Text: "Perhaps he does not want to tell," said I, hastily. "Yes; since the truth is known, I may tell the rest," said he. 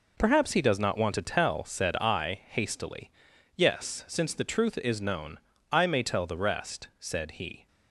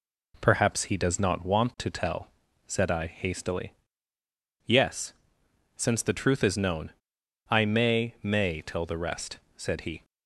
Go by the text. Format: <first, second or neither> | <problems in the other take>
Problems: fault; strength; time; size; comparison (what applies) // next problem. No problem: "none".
first | says "may" twice; at 8.2 s